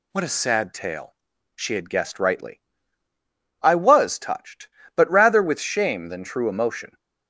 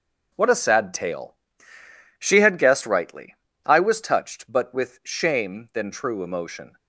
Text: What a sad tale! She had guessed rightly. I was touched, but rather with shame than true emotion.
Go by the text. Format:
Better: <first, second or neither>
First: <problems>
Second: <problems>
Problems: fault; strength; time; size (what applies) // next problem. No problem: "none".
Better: first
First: none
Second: skips "rather"; at 4.7 s